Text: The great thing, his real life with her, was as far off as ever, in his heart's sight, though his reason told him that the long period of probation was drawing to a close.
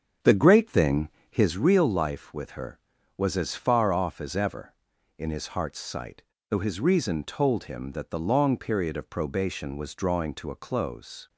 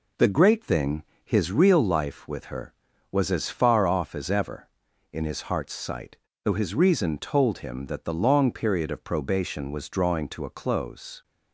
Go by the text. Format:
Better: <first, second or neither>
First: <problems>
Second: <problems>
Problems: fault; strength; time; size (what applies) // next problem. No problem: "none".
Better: second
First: starts louder than the rest; strong; until 1.5 s; 7.5 dB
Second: none